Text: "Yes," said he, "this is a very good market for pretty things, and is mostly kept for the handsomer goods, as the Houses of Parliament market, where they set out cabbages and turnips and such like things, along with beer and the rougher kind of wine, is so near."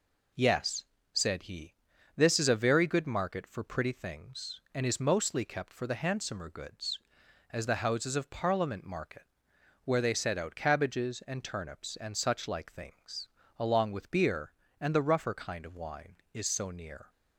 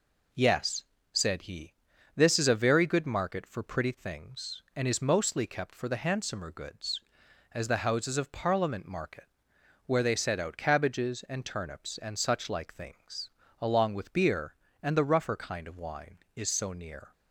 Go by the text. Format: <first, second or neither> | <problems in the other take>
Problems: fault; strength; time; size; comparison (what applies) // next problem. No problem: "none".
neither | none